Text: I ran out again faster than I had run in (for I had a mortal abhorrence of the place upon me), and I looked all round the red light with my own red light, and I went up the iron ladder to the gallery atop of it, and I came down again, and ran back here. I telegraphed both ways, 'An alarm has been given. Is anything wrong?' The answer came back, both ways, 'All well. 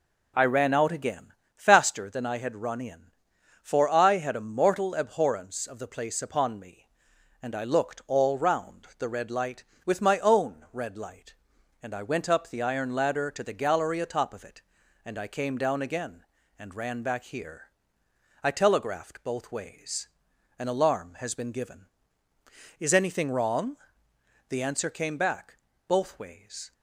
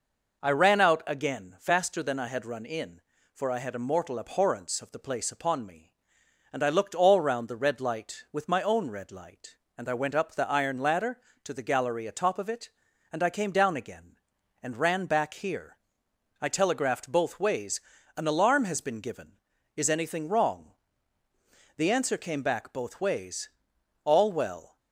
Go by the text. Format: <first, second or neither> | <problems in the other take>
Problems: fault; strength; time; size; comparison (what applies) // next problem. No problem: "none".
second | pauses between "again" and "faster"; slight; at 1.3 s; 0.22 s long // stops before "All well"; at 26.7 s